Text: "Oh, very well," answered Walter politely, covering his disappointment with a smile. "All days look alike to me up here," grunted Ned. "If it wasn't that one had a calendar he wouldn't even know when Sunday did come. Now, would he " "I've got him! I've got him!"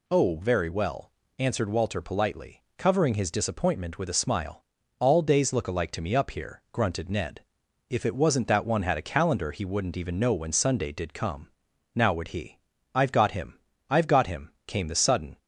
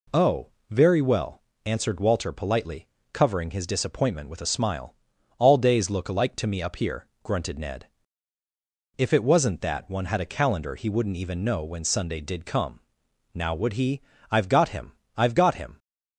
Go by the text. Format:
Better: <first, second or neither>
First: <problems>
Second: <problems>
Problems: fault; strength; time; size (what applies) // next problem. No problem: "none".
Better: second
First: goes on to say "came the sudden"; noticeable; from 14.6 s on; 0.70 s long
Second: none